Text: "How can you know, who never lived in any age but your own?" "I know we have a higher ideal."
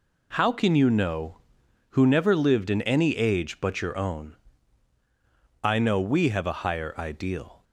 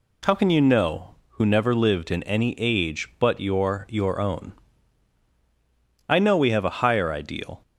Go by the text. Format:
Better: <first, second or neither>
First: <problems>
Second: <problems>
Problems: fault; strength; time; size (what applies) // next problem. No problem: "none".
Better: first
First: none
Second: says "your" twice; at 3.8 s